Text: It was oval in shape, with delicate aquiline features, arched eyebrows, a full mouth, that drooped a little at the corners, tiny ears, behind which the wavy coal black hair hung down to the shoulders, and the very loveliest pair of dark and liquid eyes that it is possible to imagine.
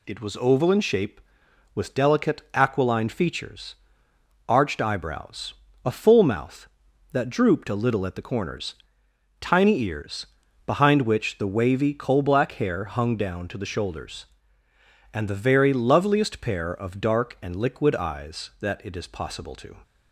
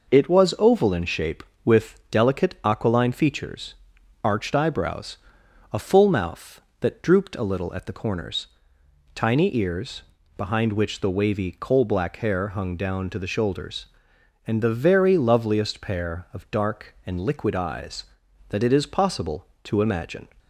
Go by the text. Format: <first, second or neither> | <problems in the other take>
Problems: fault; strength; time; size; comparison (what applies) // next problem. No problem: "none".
second | stops before "imagine"; at 19.8 s